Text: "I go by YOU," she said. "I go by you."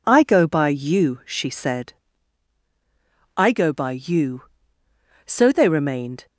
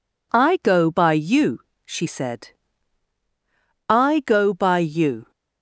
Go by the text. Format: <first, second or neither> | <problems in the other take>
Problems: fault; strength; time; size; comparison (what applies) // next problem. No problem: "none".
second | goes on to say "So they remained"; noticeable; from 5.2 s on; 1.0 s long